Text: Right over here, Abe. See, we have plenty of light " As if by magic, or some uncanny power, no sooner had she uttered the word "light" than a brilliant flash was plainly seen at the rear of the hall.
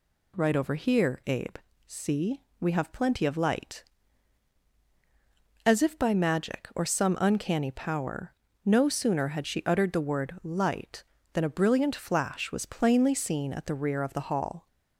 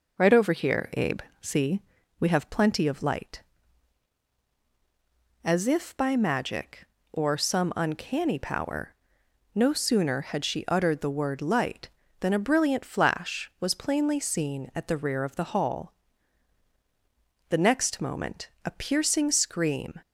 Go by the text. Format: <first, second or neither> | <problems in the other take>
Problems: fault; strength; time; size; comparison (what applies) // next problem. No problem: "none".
first | starts louder than the rest; until 1.4 s; 6.5 dB // goes on to say "The next moment a piercing scream"; strong; from 17.4 s on; 2.5 s long